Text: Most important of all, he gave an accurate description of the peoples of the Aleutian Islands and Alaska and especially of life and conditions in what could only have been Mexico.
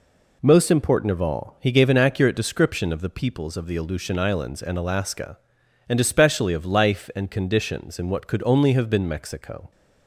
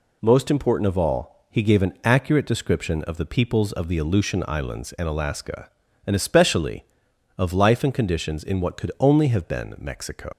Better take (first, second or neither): first